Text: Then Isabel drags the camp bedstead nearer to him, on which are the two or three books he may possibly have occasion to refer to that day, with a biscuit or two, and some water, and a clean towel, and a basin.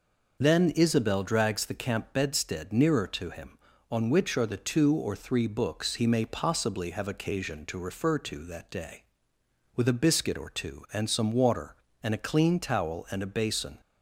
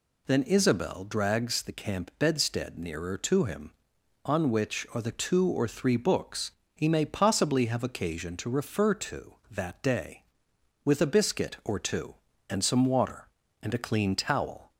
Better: first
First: none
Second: pauses between "books" and "he"; slight; at 6.5 s; 0.24 s long // stops before "and a basin"; at 14.7 s

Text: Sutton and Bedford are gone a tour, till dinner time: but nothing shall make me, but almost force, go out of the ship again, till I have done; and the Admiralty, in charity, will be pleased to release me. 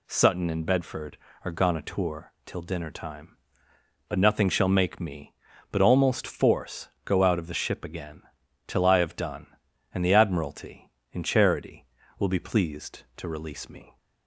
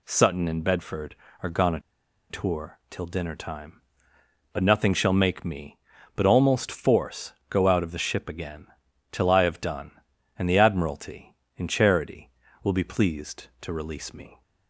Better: first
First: none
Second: pauses between "a" and "tour"; noticeable; at 1.7 s; 0.50 s long

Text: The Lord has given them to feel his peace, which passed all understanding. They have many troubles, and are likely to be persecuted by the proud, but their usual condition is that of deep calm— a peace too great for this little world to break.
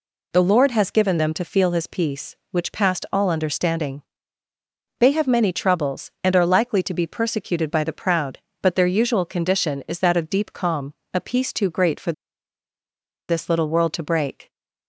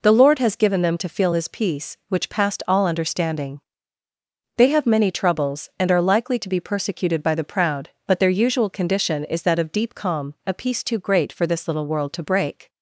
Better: second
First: pauses between "for" and "this"; at 12.1 s; 1.1 s long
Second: none

